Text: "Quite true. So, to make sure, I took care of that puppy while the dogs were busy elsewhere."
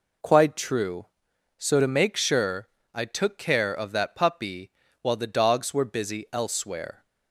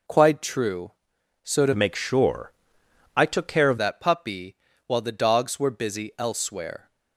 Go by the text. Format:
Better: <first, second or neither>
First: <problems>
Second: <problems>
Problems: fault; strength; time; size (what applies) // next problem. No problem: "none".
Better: first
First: pauses between "puppy" and "while"; slight; at 4.6 s; 0.32 s long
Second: changes voice from "make" to "of"; from 1.7 to 3.7 s; 2.0 s long // pauses between "puppy" and "while"; slight; at 4.5 s; 0.32 s long